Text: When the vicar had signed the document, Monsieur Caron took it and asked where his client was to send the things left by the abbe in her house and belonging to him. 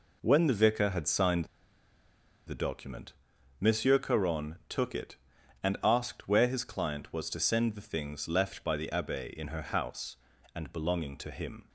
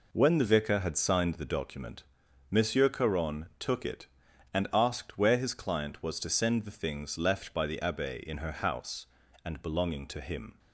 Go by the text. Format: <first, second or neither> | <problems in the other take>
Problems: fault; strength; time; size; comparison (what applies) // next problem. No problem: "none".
second | pauses between "signed" and "the"; at 1.4 s; 1.0 s long